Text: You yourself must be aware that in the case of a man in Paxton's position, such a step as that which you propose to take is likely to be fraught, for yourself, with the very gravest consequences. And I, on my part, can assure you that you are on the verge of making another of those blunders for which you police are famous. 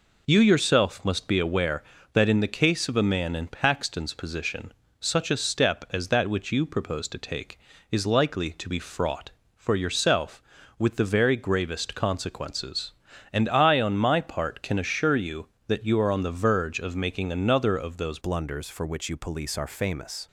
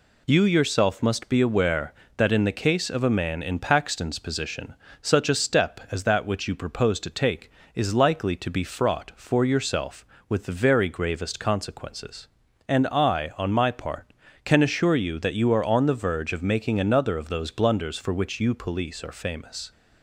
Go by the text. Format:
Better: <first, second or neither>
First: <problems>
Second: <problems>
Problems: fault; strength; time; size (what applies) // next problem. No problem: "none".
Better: second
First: changes voice at "blunders"; from 18.1 s on; 2.1 s long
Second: none